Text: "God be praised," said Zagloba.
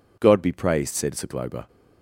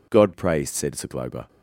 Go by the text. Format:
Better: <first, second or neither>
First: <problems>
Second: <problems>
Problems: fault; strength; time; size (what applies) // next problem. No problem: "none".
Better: first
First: none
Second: skips "be"; at 0.3 s